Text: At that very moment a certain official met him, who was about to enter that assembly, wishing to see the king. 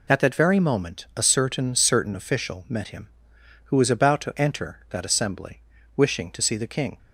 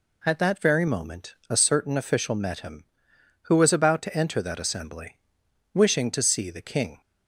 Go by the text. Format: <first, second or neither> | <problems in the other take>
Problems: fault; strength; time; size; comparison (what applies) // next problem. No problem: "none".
second | says "certain" twice; at 1.7 s